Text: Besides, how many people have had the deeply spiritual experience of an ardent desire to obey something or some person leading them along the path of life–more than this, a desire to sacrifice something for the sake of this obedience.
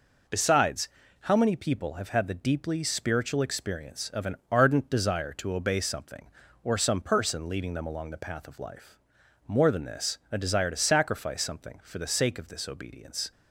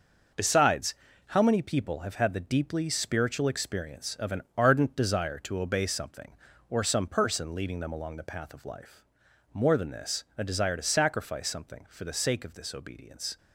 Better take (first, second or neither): first